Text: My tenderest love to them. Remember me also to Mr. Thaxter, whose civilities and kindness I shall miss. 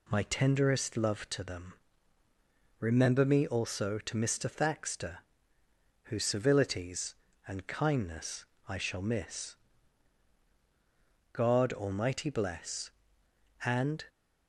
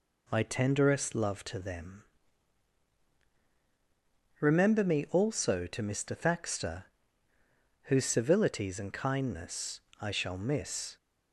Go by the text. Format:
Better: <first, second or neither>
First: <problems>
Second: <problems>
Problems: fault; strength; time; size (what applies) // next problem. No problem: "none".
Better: second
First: pauses between "kindness" and "I"; slight; at 8.4 s; 0.24 s long // goes on to say "God Almighty bless and"; strong; from 11.3 s on; 2.7 s long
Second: pauses between "kindness" and "I"; slight; at 9.7 s; 0.22 s long